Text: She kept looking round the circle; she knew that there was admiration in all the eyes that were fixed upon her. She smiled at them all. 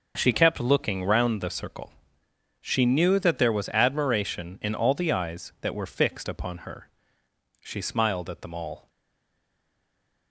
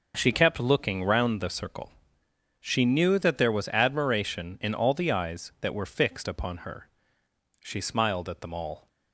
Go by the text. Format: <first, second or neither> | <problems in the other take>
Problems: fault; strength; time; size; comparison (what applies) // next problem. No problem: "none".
second | stays silent after the last word; noticeable; from 8.8 s on; 1.5 s long